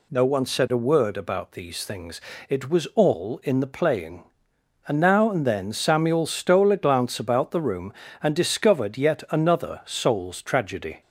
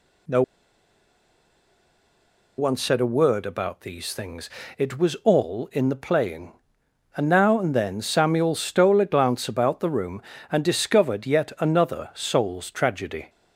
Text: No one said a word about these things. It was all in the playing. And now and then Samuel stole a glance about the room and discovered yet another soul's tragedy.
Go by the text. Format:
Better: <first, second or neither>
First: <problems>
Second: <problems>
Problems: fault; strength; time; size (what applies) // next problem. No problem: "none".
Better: first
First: none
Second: pauses between "No" and "one"; strong; at 0.4 s; 2.1 s long